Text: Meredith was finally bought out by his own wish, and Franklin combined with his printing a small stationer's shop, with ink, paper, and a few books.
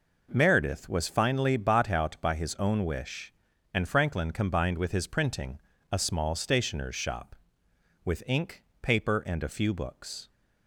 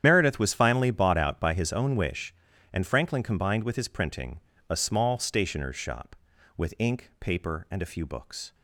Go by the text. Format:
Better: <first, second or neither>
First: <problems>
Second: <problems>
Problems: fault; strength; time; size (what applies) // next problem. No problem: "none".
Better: first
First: pauses between "printing" and "a"; slight; at 5.5 s; 0.34 s long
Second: loses the start of "Meredith"; at 0.0 s; 80 ms // starts louder than the rest; strong; until 1.0 s; 9.5 dB // pauses between "printing" and "a"; slight; at 4.4 s; 0.28 s long